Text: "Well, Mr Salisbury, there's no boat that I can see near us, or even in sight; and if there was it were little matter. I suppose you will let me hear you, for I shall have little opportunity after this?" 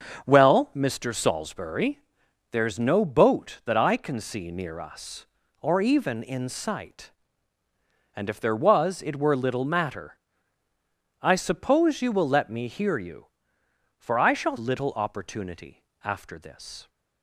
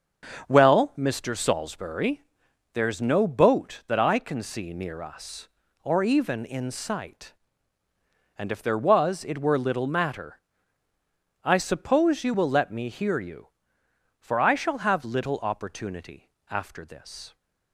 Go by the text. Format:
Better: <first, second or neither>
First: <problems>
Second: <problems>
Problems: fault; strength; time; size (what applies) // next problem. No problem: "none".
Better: second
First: starts louder than the rest; strong; until 1.3 s; 7 dB // skips "have"; at 14.5 s // pauses between "opportunity" and "after"; slight; at 15.8 s; 0.20 s long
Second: starts louder than the rest; strong; until 1.5 s; 7 dB // pauses between "opportunity" and "after"; slight; at 16.2 s; 0.20 s long